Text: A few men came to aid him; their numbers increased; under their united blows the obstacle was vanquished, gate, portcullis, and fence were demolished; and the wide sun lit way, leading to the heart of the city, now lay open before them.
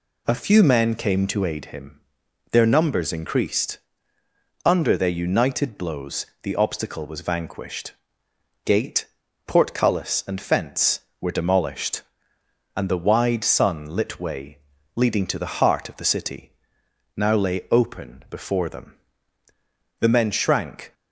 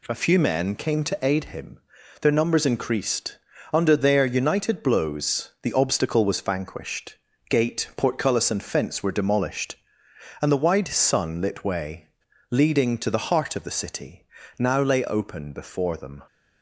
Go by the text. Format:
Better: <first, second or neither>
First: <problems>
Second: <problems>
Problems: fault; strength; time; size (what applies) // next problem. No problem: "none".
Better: second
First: pauses between "blows" and "the"; slight; at 6.2 s; 0.16 s long // goes on to say "The men shrank"; noticeable; from 19.9 s on; 0.94 s long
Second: none